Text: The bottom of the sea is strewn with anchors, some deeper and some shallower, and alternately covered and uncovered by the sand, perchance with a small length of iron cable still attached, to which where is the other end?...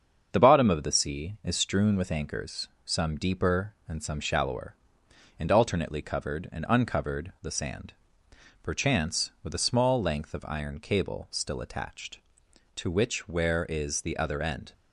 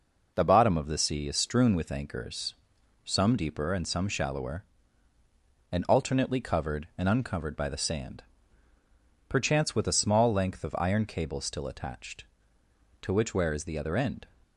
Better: second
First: starts louder than the rest; strong; until 1.3 s; 7 dB // skips "by"; at 7.3 s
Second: none

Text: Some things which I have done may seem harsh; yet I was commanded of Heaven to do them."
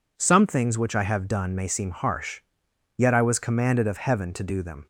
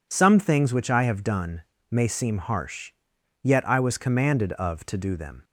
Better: first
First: none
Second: pauses between "done" and "may"; slight; at 1.6 s; 0.28 s long // skips "Heaven"; at 4.8 s

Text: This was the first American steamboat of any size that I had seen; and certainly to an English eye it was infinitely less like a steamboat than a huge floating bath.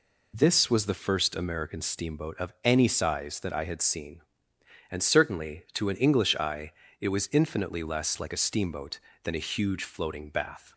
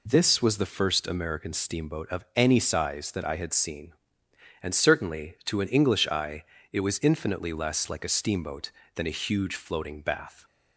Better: neither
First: pauses between "eye" and "it"; slight; at 6.7 s; 0.26 s long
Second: pauses between "eye" and "it"; slight; at 6.4 s; 0.26 s long

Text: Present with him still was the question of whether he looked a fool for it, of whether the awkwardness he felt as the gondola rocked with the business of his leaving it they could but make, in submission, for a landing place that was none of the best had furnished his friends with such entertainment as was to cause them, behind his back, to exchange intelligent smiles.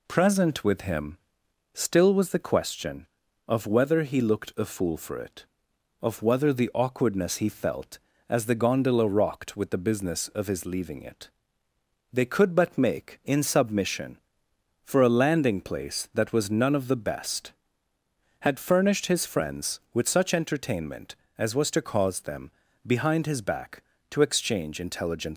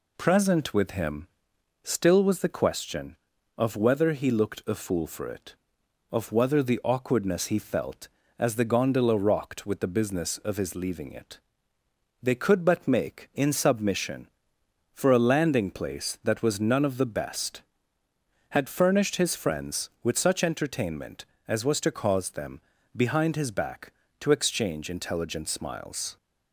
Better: second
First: pauses between "him" and "still"; noticeable; at 1.1 s; 0.56 s long // pauses between "it" and "they"; noticeable; at 11.2 s; 0.86 s long // stops before "smiles"; at 25.3 s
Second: pauses between "him" and "still"; noticeable; at 1.2 s; 0.56 s long // pauses between "it" and "they"; noticeable; at 11.3 s; 0.86 s long

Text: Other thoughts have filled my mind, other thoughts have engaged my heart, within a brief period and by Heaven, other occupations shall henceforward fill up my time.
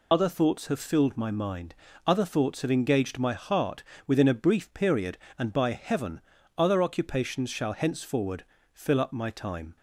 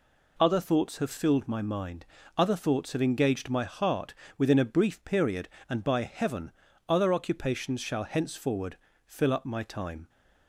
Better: second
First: loses the start of "Other"; at 0.1 s; 65 ms // pauses between "henceforward" and "fill"; slight; at 8.4 s; 0.30 s long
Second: pauses between "henceforward" and "fill"; slight; at 8.7 s; 0.30 s long

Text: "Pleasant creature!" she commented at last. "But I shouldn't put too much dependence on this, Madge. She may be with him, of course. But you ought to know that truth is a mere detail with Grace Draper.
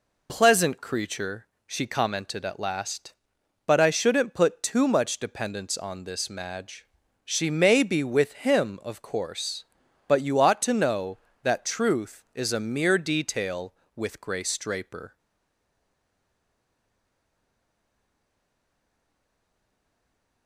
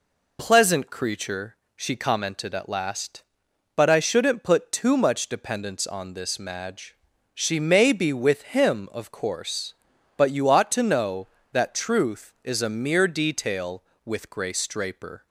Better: second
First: stays silent after the last word; strong; from 15.1 s on; 5.3 s long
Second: none

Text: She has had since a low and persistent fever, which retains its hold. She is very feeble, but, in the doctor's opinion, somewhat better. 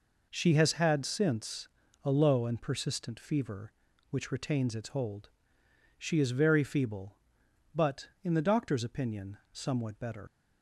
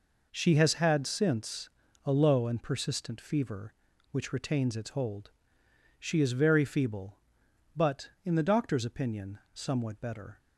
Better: second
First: pauses between "since" and "a"; slight; at 1.6 s; 0.34 s long // leaves "better" unfinished; at 10.2 s; 95 ms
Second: pauses between "since" and "a"; slight; at 1.6 s; 0.34 s long

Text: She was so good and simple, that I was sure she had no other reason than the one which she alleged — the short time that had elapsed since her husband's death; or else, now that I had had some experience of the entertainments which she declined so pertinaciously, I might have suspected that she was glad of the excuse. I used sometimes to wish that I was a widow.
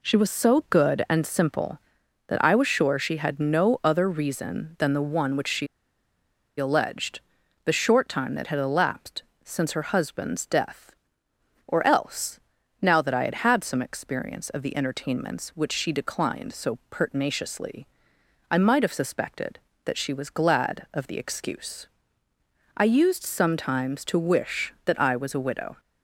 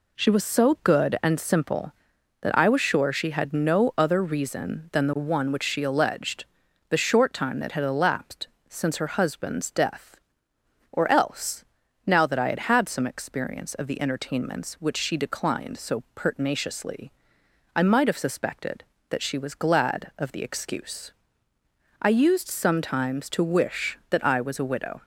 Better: second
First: pauses between "she" and "alleged"; noticeable; at 5.6 s; 0.92 s long // pauses between "elapsed" and "since"; slight; at 9.2 s; 0.20 s long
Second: pauses between "elapsed" and "since"; slight; at 8.4 s; 0.20 s long

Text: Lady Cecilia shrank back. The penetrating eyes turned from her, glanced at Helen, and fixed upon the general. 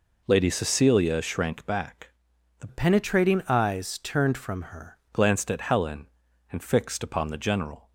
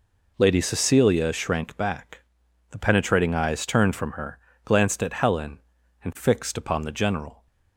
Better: second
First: changes voice from "penetrating" to "her"; from 2.6 to 4.9 s; 2.3 s long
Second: none

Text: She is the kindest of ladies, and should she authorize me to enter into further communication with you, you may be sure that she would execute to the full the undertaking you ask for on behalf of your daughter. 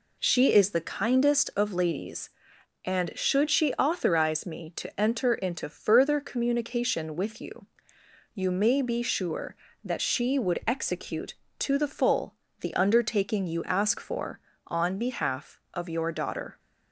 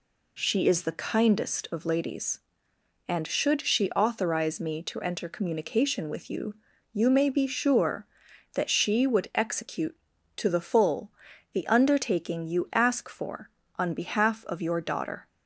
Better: first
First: pauses between "full" and "the"; slight; at 12.3 s; 0.26 s long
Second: skips "into further"; at 5.2 s // pauses between "full" and "the"; at 11.0 s; 0.44 s long

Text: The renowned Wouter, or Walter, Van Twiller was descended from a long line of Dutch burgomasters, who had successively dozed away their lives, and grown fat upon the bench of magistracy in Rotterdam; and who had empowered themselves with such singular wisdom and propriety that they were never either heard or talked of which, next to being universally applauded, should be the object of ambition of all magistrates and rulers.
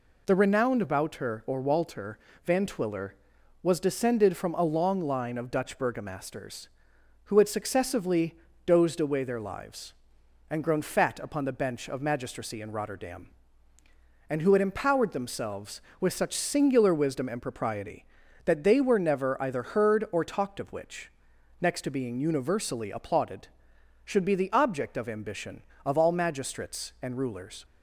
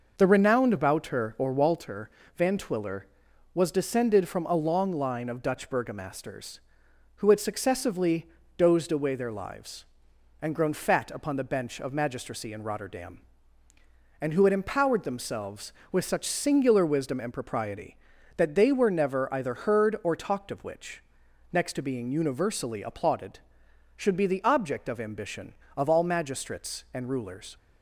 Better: first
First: pauses between "successively" and "dozed"; slight; at 8.3 s; 0.28 s long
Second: starts louder than the rest; noticeable; until 1.8 s; 5.5 dB // pauses between "successively" and "dozed"; slight; at 8.2 s; 0.28 s long

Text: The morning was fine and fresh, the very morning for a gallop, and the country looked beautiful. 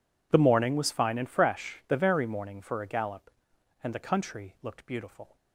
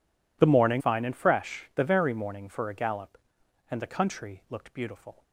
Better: first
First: none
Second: skips "was"; at 0.8 s

